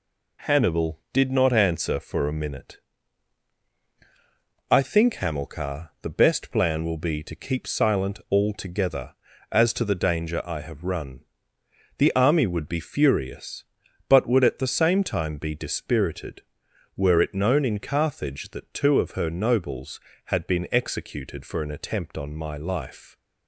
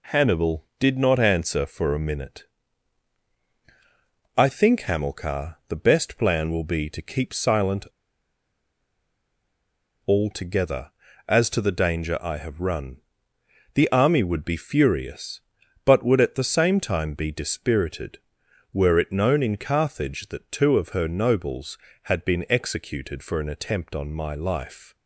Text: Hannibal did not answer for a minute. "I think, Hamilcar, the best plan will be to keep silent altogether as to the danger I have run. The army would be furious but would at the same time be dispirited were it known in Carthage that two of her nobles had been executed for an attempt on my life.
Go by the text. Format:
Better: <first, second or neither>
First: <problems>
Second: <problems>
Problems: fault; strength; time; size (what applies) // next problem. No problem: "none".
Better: first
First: none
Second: pauses between "silent" and "altogether"; strong; at 7.8 s; 2.2 s long